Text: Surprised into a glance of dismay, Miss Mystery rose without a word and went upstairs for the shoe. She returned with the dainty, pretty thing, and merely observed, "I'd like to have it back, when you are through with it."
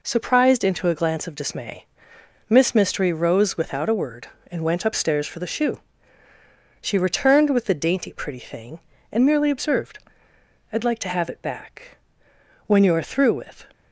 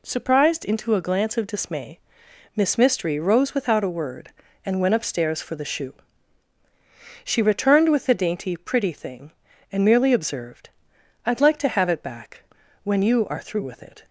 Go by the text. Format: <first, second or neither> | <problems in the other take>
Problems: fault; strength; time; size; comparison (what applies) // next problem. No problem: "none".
second | stops before "it"; at 13.7 s